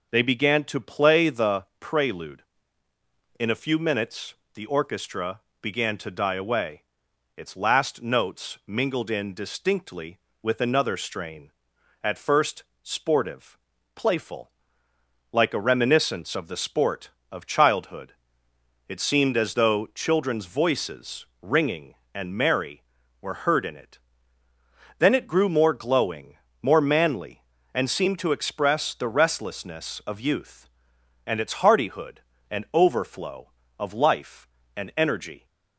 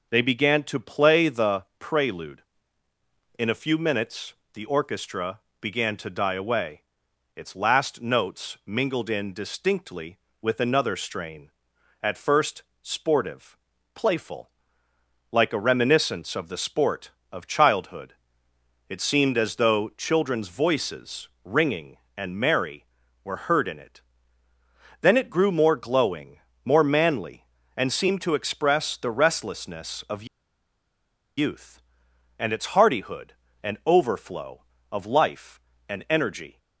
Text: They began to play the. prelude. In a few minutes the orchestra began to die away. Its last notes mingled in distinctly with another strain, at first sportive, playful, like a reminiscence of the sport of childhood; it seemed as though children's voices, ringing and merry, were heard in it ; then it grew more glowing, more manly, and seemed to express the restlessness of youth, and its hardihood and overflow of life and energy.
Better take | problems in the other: first | pauses between "minutes" and "the"; slight; at 4.3 s; 0.20 s long; slight in the first // pauses between "orchestra" and "began"; slight; at 5.4 s; 0.20 s long; slight in the first // pauses between "first" and "sportive"; slight; at 12.6 s; 0.18 s long; slight in the first // pauses between "of" and "youth"; at 30.2 s; 1.1 s long

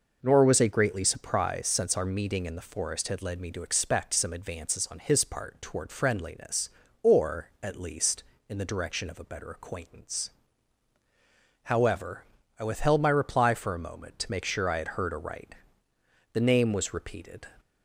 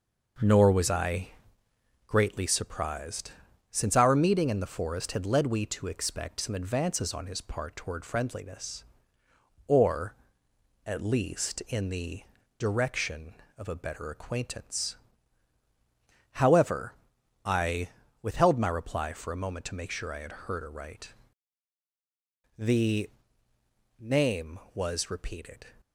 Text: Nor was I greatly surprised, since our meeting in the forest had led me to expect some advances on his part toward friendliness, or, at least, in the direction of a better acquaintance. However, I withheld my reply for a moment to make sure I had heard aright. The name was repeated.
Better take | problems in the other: first | pauses between "I" and "greatly"; noticeable; at 1.3 s; 0.74 s long // says "we" for "me"; at 5.4 s // pauses between "the" and "direction"; at 12.2 s; 0.38 s long // pauses between "I" and "withheld"; slight; at 17.8 s; 0.32 s long // pauses between "The" and "name"; noticeable; at 23.0 s; 0.90 s long

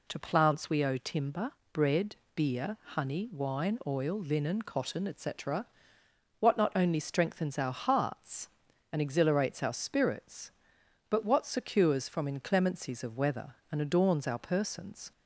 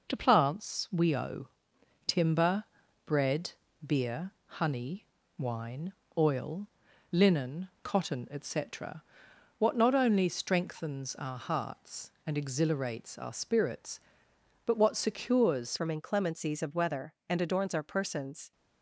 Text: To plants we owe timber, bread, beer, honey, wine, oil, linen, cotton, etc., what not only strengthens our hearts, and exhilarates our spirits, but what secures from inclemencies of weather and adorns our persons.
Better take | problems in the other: first | pauses between "owe" and "timber"; noticeable; at 1.4 s; 0.58 s long // changes voice at "from"; from 15.7 s on; 2.8 s long

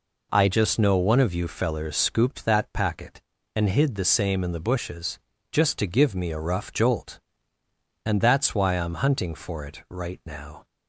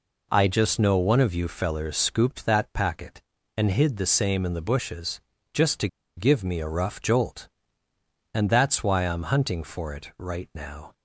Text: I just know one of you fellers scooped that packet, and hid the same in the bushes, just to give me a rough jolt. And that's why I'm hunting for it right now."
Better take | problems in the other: first | pauses between "to" and "give"; slight; at 5.8 s; 0.29 s long

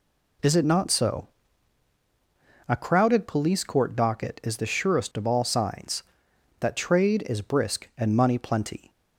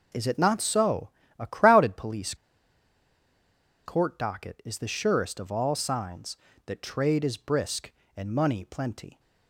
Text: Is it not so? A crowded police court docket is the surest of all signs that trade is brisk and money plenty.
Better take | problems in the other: first | pauses between "police" and "court"; strong; at 2.3 s; 1.5 s long

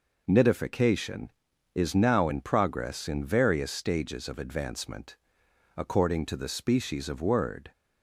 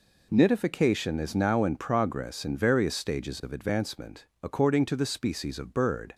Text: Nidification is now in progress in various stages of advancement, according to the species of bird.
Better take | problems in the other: second | says "word" for "bird"; at 7.2 s

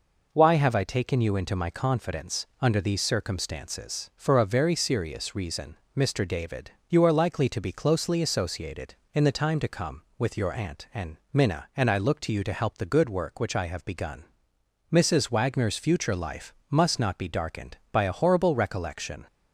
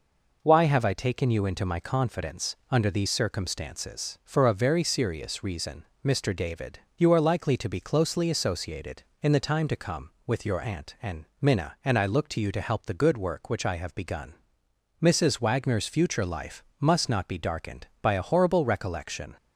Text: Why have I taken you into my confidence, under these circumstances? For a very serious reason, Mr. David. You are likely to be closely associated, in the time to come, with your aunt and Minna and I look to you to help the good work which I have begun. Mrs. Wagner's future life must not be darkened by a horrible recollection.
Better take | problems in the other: neither | pauses between "and" and "Minna"; slight; the same in both // pauses between "life" and "must"; slight; the same in both

